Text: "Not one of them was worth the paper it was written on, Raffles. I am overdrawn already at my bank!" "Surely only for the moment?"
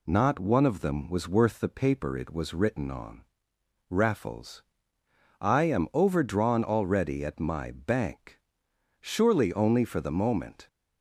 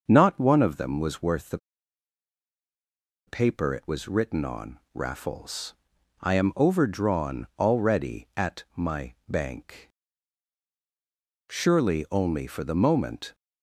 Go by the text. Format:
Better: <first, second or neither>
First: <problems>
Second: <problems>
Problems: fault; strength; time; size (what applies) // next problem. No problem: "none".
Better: first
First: none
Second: starts louder than the rest; noticeable; until 1.0 s; 6 dB // pauses between "the" and "paper"; strong; at 1.5 s; 1.6 s long